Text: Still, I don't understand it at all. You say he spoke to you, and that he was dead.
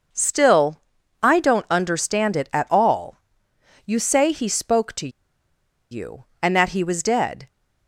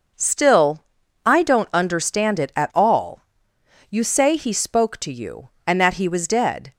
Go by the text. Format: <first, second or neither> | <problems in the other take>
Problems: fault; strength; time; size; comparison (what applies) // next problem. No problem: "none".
second | pauses between "to" and "you"; noticeable; at 5.0 s; 0.82 s long